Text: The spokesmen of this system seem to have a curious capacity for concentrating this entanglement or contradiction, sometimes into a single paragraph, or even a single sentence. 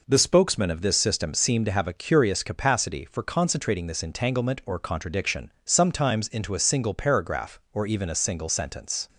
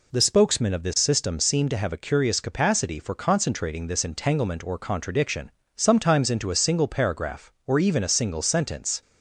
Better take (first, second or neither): neither